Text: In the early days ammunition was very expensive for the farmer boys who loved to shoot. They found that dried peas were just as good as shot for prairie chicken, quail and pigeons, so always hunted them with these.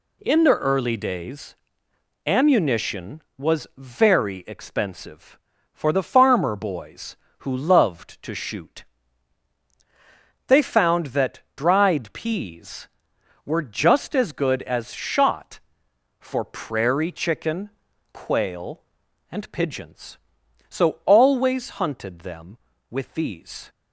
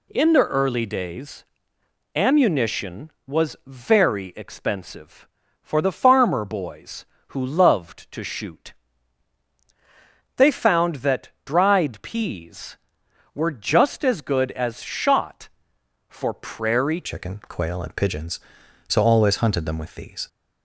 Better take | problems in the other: first | pauses between "days" and "ammunition"; noticeable; at 1.4 s; 0.72 s long; noticeable in the first // pauses between "that" and "dried"; slight; at 11.2 s; 0.16 s long; slight in the first // changes voice at "chicken"; from 17.0 s on; 3.2 s long

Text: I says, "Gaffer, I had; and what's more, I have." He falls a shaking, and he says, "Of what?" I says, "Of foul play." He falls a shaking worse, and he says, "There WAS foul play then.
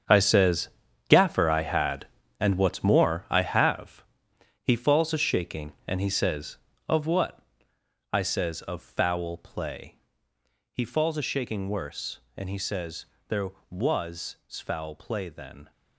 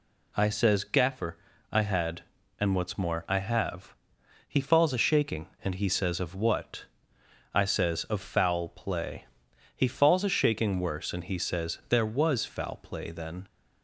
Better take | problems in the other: second | gets quieter; strong; throughout; 12.5 dB

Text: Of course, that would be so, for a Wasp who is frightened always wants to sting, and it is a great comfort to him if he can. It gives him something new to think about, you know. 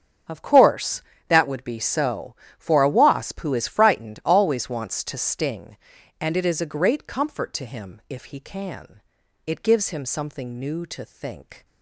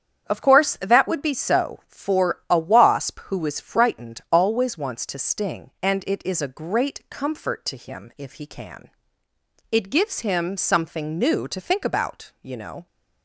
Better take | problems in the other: second | starts louder than the rest; until 1.5 s; 7 dB; strong in the second // stops before "about you know"; at 11.6 s

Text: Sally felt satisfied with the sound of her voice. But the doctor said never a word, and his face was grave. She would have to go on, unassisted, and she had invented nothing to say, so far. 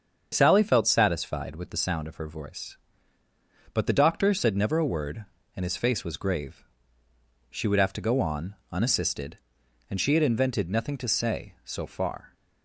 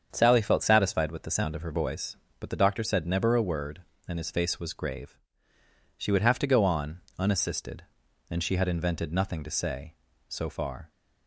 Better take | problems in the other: neither | starts louder than the rest; strong; the same in both

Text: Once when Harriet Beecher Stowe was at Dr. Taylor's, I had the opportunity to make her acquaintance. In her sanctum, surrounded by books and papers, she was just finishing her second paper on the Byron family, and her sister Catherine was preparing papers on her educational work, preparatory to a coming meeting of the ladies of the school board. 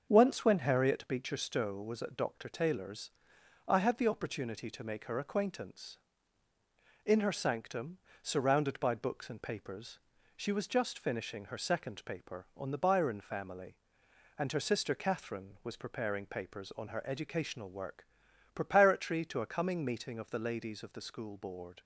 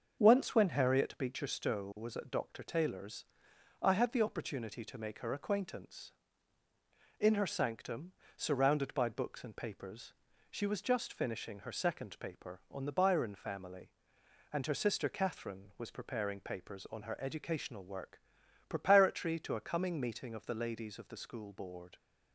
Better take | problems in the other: neither | starts louder than the rest; the same in both

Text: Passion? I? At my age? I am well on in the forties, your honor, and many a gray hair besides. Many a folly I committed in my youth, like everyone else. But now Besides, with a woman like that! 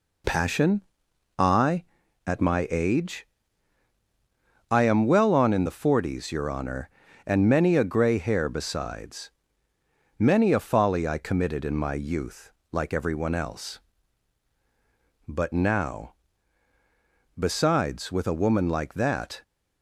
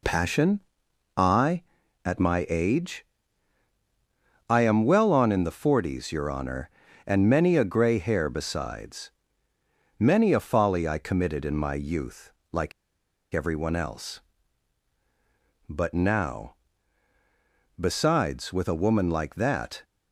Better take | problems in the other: first | pauses between "like" and "everyone"; noticeable; at 12.7 s; 0.61 s long // pauses between "now" and "Besides"; strong; at 16.5 s; 1.2 s long; strong in the first

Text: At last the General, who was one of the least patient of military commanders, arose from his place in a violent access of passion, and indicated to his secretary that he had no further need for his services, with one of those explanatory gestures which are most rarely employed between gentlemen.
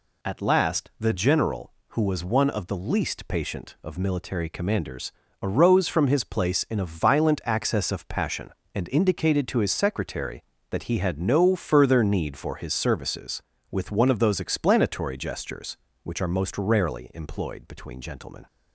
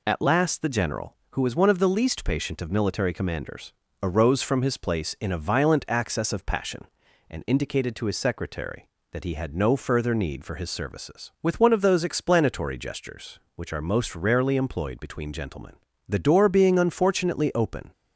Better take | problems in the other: first | goes on to say "The door being unfortunately open"; strong; from 16.0 s on; 1.8 s long

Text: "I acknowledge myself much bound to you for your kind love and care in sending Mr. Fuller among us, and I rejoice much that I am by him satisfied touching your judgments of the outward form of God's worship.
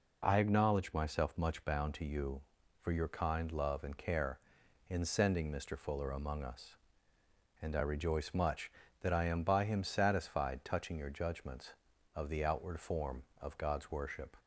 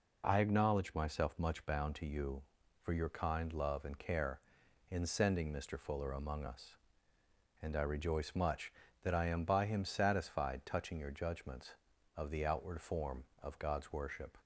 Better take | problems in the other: neither | none

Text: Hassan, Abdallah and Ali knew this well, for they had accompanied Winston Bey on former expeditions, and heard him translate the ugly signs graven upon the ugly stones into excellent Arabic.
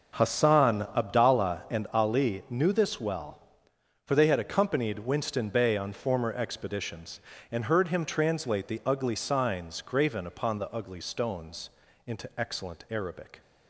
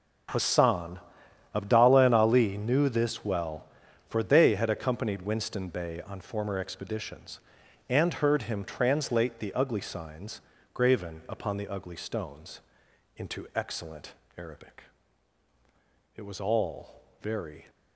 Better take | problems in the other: first | pauses between "signs" and "graven"; slight; at 10.3 s; 0.32 s long // pauses between "stones" and "into"; noticeable; at 12.5 s; 0.56 s long; slight in the first // pauses between "excellent" and "Arabic"; slight; at 14.1 s; 0.24 s long // goes on to say "It was all very"; from 16.1 s on; 1.5 s long

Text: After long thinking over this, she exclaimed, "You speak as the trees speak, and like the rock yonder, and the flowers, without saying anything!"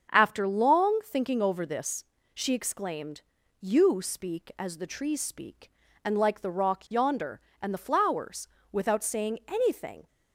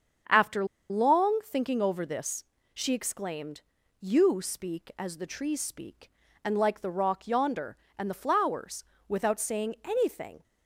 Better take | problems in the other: first | starts louder than the rest; strong; until 1.5 s; 7.5 dB; also in the first // pauses between "After" and "long"; slight; at 0.6 s; 0.25 s long

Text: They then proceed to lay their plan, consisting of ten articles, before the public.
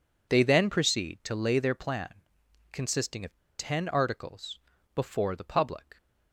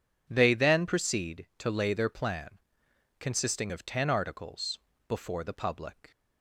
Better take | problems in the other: second | pauses between "of" and "ten"; slight; at 3.3 s; 0.21 s long

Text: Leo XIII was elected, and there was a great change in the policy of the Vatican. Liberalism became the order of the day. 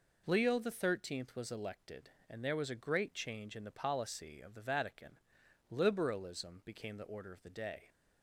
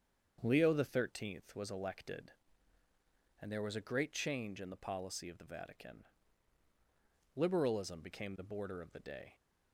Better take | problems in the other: first | starts louder than the rest; strong; until 1.4 s; 7 dB // says "border" for "order"; at 8.4 s

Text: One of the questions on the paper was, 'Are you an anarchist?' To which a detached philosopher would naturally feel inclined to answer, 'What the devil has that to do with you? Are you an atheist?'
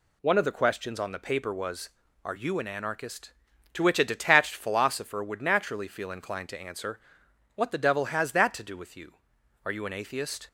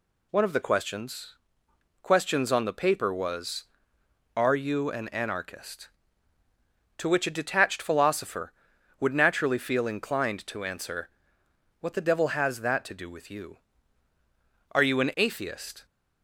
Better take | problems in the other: first | says "questions" twice; at 2.0 s

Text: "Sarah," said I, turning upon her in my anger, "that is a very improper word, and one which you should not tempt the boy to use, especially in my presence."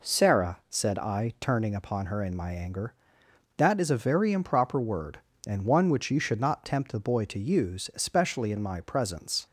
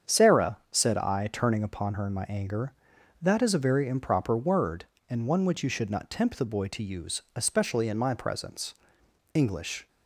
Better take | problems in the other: first | starts louder than the rest; strong; until 1.1 s; 7.5 dB // goes on to say "English"; from 9.3 s on; 0.54 s long

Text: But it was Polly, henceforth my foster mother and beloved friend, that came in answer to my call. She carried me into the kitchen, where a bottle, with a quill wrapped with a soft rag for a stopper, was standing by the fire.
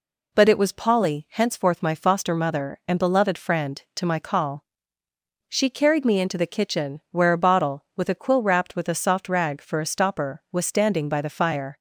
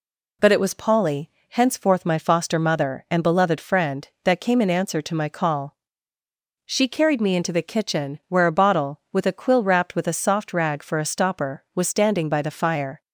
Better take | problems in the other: second | skips "that came in answer"; at 3.8 s

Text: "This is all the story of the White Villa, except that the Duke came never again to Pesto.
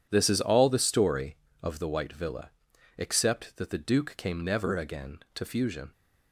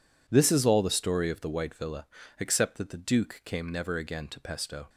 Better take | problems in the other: second | says "Fusion" for "Pesto"; at 5.4 s

